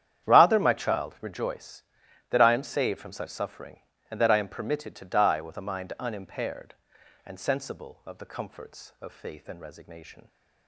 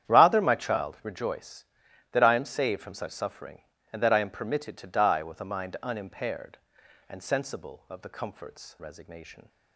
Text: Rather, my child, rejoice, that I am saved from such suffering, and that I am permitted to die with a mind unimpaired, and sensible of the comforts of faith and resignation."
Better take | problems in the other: first | starts louder than the rest; strong; until 1.1 s; 10 dB; strong in the first // skips "of faith and"; at 8.7 s

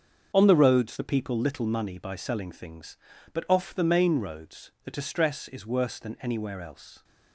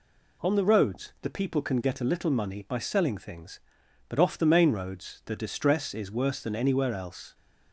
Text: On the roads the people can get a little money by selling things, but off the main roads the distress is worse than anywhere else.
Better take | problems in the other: second | starts louder than the rest; until 1.3 s; 7 dB // skips "can get a"; at 1.3 s

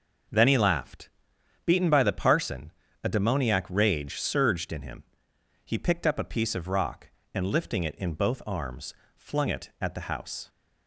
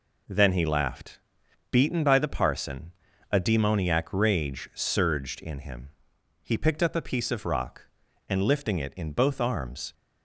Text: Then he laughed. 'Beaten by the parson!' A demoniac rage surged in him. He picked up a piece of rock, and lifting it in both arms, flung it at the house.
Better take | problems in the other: first | stops before "flung it at the house"; at 9.9 s

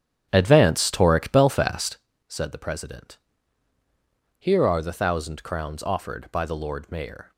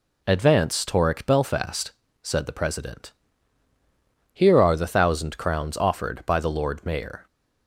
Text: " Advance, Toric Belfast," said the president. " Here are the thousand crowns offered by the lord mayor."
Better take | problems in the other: second | starts louder than the rest; strong; until 2.1 s; 8 dB

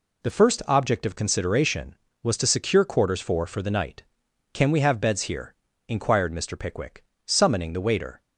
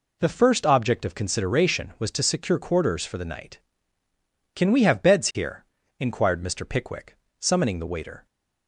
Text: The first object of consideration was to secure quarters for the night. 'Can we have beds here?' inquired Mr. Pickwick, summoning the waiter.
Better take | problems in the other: second | says "for" twice; at 3.4 s

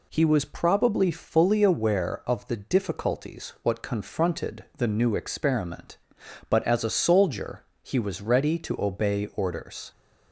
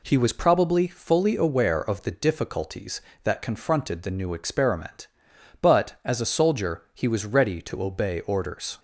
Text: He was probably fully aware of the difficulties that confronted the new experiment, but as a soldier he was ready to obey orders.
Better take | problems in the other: second | says "what" for "that"; at 3.6 s // pauses between "soldier" and "he"; slight; at 7.6 s; 0.22 s long

